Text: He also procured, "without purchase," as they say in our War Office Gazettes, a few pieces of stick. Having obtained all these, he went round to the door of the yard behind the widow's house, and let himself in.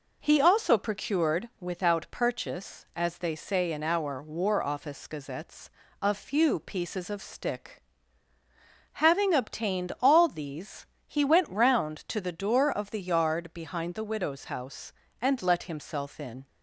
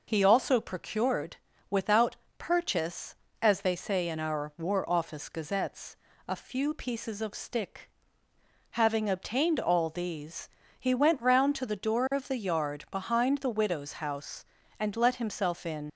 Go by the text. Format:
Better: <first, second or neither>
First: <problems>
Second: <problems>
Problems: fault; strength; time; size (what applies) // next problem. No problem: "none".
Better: first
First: none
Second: pauses between "without" and "purchase"; slight; at 2.1 s; 0.24 s long // leaves "in" unfinished; at 15.8 s; 70 ms